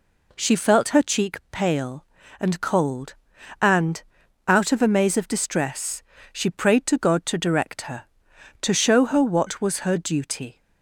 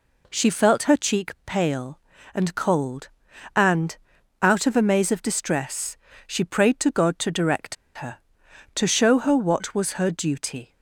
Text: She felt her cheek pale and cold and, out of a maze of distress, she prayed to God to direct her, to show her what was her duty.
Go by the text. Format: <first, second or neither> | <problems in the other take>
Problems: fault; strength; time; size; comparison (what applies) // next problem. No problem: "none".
first | pauses between "direct" and "her"; slight; at 7.7 s; 0.20 s long